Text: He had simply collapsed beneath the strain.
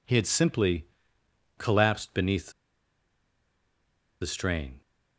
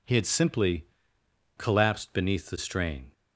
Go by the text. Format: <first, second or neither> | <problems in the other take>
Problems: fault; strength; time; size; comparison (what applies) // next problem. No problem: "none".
second | pauses between "simply" and "collapsed"; noticeable; at 0.8 s; 0.70 s long; noticeable in the second // pauses between "beneath" and "the"; strong; at 2.5 s; 1.7 s long